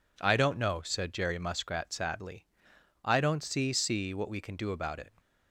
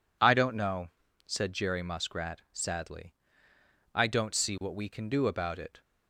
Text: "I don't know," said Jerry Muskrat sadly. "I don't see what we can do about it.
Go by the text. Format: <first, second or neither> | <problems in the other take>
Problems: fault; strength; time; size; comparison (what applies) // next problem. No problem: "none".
second | says "see" twice; at 3.7 s